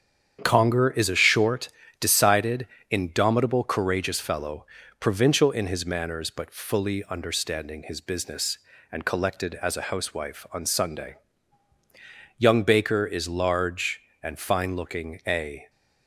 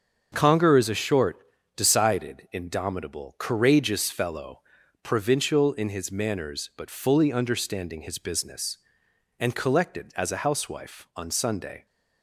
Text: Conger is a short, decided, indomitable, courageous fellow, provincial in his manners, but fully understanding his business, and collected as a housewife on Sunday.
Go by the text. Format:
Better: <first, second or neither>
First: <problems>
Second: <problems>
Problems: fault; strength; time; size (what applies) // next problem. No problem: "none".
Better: second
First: starts louder than the rest; strong; until 1.4 s; 8.5 dB // goes on to say "Young Baker is large and fine looking a"; strong; from 12.3 s on; 3.3 s long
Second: starts louder than the rest; until 1.3 s; 6.5 dB